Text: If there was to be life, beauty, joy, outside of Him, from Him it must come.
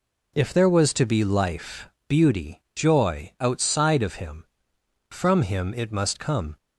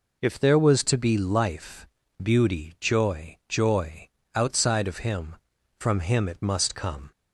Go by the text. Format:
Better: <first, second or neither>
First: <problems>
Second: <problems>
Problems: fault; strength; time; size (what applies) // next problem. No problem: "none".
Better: first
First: none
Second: says "joy" twice; at 3.4 s